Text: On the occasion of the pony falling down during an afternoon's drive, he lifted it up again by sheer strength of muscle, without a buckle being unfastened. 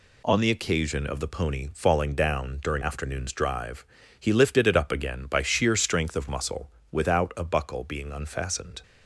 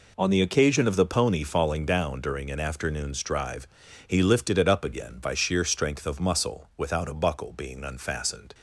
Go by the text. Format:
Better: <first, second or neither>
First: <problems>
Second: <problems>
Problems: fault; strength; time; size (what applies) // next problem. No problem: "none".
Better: second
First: skips "an"; at 2.8 s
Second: none